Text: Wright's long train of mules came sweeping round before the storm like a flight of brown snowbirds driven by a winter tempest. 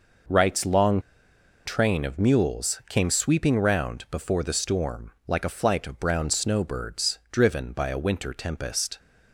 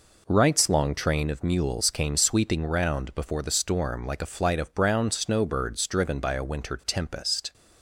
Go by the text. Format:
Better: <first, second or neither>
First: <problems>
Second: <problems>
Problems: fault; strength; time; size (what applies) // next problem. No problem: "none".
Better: second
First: pauses between "long" and "train"; noticeable; at 0.9 s; 0.66 s long // pauses between "storm" and "like"; slight; at 5.1 s; 0.16 s long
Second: none